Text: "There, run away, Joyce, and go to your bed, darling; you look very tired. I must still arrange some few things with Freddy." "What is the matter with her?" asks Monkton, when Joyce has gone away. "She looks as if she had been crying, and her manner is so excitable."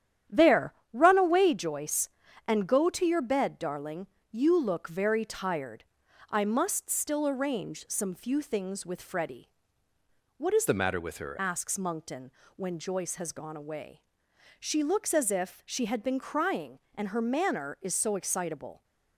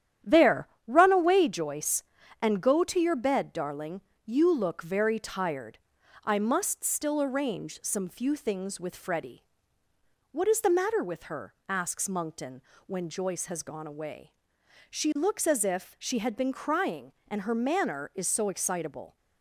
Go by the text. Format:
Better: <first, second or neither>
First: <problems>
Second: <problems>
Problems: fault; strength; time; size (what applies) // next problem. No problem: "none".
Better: second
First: starts louder than the rest; strong; until 1.4 s; 10.5 dB // changes voice from "the" to "her"; from 10.6 to 11.3 s; 0.7 s long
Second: starts louder than the rest; strong; until 1.4 s; 10.5 dB